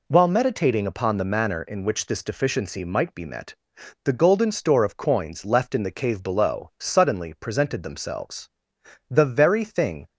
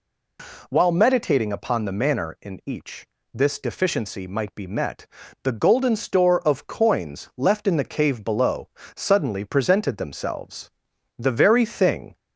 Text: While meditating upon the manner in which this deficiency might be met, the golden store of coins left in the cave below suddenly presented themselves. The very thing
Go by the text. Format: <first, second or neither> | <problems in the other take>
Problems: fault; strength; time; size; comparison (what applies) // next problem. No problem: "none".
first | says "each" for "which"; at 2.6 s // pauses between "below" and "suddenly"; slight; at 8.6 s; 0.26 s long